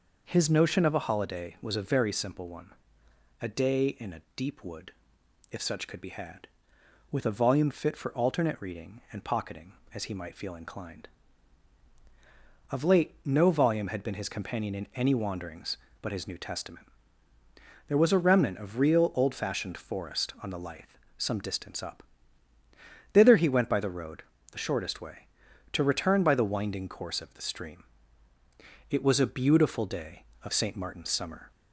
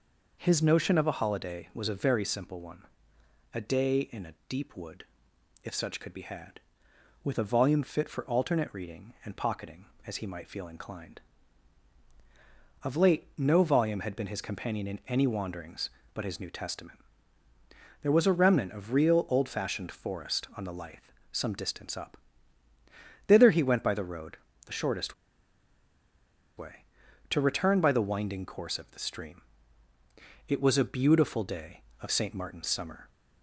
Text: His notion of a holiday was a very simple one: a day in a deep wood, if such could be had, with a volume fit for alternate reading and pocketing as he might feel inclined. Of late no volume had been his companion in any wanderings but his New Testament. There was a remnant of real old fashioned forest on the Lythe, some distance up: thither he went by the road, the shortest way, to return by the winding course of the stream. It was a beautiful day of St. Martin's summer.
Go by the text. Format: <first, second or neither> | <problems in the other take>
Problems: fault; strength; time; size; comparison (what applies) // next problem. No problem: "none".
first | pauses between "shortest" and "way"; strong; at 25.1 s; 1.4 s long